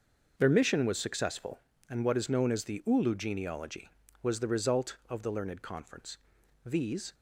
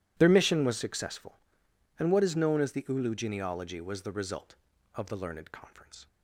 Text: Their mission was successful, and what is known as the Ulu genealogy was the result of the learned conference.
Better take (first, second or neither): second